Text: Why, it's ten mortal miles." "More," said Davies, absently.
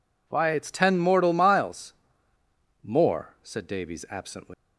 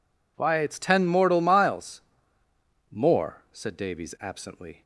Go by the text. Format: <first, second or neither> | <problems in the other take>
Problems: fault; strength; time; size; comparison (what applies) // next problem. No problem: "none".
second | leaves "absently" unfinished; at 4.5 s; 175 ms